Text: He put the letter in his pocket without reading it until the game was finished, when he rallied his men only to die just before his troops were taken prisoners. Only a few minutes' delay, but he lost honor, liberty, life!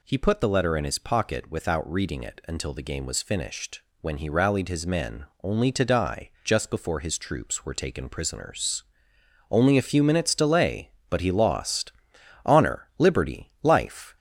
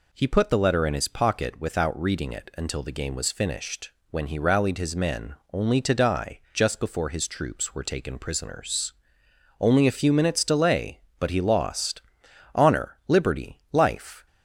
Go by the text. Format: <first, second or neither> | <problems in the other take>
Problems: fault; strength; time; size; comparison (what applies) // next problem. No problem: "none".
second | gets louder; slight; throughout; 3.5 dB // pauses between "men" and "only"; slight; at 5.2 s; 0.18 s long; slight in the second // pauses between "lost" and "honor"; noticeable; at 11.9 s; 0.52 s long; noticeable in the second